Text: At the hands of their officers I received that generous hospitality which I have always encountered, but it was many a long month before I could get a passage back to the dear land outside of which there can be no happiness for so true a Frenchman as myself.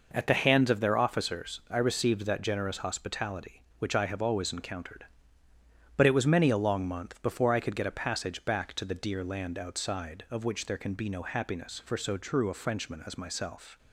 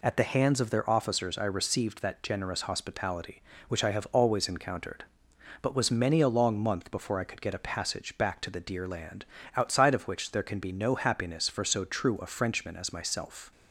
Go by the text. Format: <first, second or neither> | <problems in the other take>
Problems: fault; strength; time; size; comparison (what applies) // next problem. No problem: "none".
first | skips "it"; at 5.7 s // pauses between "land" and "outside"; slight; at 9.2 s; 0.30 s long